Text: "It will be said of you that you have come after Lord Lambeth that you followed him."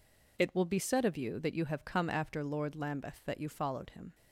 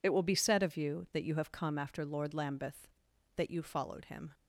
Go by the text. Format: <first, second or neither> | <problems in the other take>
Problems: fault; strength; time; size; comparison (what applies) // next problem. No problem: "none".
neither | none